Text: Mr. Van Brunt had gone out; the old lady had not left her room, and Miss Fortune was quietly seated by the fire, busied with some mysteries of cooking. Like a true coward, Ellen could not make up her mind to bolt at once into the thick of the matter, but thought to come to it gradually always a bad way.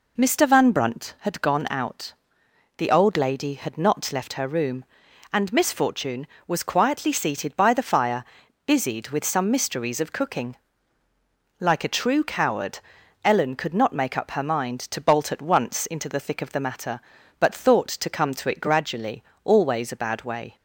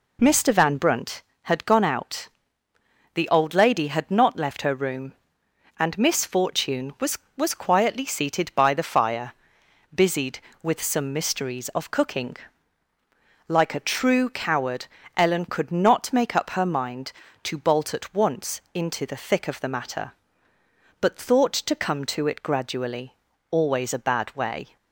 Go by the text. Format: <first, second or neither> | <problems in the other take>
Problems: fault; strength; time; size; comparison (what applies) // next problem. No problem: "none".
first | says "was" twice; at 7.3 s // pauses between "gradually" and "always"; slight; at 23.1 s; 0.36 s long; slight in the first